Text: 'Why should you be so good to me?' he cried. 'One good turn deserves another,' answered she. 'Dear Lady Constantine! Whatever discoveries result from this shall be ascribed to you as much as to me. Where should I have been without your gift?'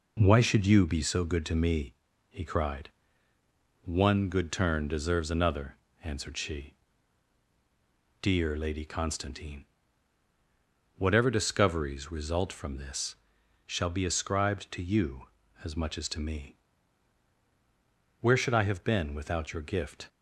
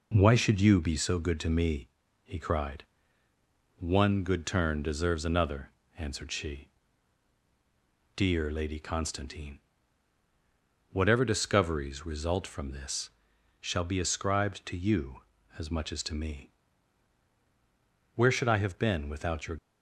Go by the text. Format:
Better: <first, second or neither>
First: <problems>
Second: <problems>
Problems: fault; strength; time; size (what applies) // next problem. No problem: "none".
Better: first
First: pauses between "this" and "shall"; noticeable; at 13.1 s; 0.50 s long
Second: pauses between "this" and "shall"; noticeable; at 13.0 s; 0.50 s long // stops before "gift"; at 19.5 s